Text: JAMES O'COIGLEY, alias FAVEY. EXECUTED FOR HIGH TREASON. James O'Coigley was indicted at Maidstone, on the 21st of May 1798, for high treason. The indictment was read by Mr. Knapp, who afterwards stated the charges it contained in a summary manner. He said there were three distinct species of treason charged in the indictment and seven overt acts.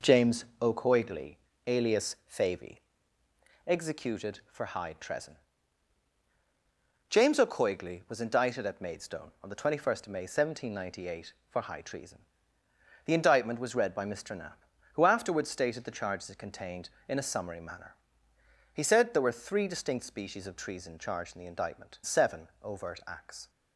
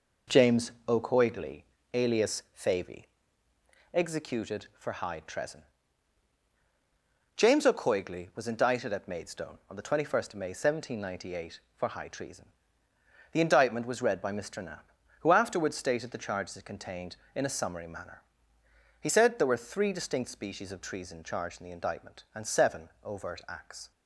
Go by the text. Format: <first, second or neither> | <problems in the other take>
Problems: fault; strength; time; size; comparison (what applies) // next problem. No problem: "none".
second | skips "and"; at 22.0 s // pauses between "seven" and "overt"; slight; at 22.4 s; 0.16 s long; slight in the second